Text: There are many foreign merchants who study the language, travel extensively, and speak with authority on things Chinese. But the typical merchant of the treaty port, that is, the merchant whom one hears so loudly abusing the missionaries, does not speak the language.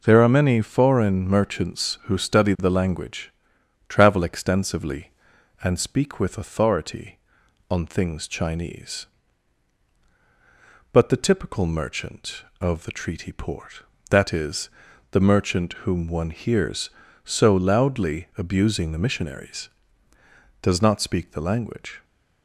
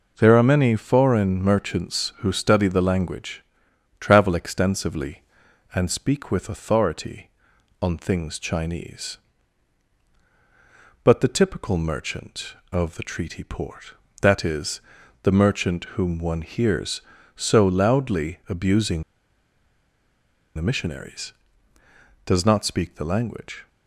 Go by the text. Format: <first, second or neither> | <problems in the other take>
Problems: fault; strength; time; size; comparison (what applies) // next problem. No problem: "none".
first | pauses between "abusing" and "the"; strong; at 19.0 s; 1.5 s long